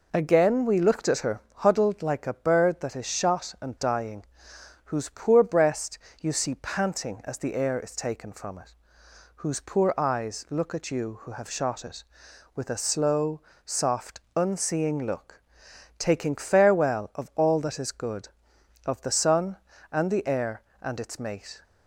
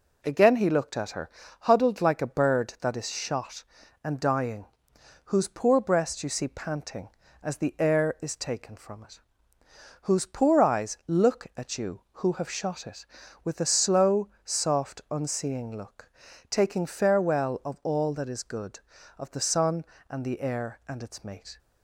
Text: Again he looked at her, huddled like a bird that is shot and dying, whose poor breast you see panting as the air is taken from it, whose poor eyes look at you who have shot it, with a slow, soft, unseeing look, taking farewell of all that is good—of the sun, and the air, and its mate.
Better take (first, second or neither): second